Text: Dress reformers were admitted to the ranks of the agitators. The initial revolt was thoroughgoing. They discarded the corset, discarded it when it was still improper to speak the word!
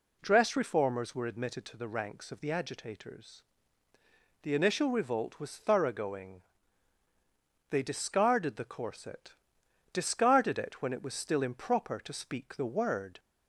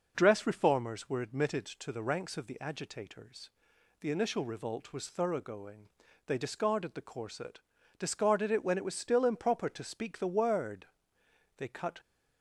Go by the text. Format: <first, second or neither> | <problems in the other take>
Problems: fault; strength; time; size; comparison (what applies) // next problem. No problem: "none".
first | goes on to say "They cut"; slight; from 11.5 s on; 0.42 s long